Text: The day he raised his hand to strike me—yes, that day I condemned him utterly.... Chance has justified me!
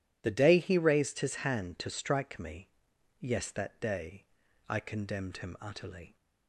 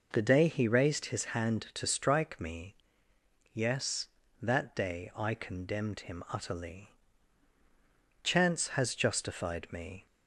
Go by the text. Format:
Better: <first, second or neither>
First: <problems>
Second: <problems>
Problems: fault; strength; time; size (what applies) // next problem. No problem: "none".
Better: second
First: pauses between "day" and "I"; at 4.2 s; 0.44 s long // stops before "Chance has justified me"; at 6.1 s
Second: none